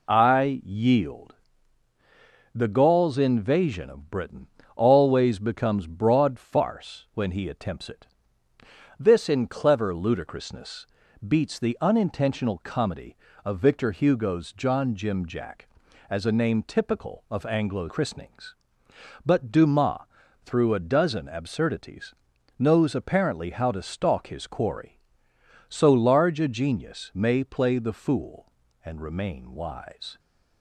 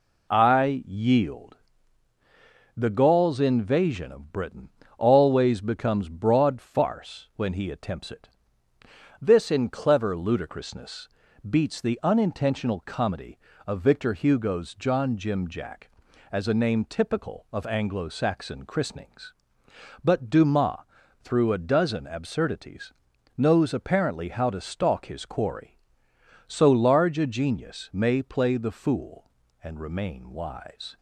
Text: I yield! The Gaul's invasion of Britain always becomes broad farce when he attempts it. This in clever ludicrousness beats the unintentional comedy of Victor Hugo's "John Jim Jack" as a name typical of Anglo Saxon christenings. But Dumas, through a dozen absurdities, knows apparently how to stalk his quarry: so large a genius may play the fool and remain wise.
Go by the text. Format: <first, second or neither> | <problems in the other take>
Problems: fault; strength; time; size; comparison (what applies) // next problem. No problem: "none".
second | pauses between "Britain" and "always"; slight; at 4.4 s; 0.28 s long; slight in the second // pauses between "ludicrousness" and "beats"; at 10.8 s; 0.42 s long; also in the second // skips "Saxon"; at 17.8 s